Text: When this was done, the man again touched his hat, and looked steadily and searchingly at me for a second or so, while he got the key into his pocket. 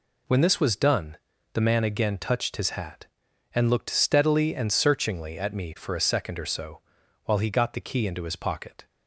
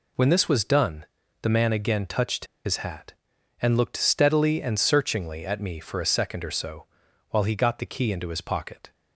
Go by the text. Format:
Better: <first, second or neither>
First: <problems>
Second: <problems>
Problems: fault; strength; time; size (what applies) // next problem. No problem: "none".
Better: first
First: none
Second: pauses between "touched" and "his"; slight; at 2.4 s; 0.19 s long